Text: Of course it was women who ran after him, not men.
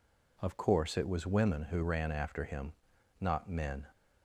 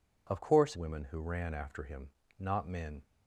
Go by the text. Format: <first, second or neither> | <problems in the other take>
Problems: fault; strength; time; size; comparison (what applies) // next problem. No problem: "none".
first | skips "it was"; at 0.7 s